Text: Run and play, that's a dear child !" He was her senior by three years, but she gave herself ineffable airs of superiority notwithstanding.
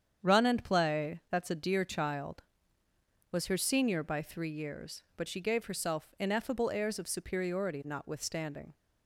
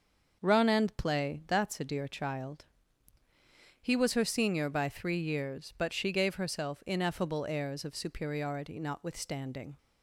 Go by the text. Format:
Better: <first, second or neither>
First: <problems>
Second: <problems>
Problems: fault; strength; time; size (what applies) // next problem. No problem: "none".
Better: second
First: starts louder than the rest; strong; until 1.3 s; 8 dB // skips "He"; at 3.3 s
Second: none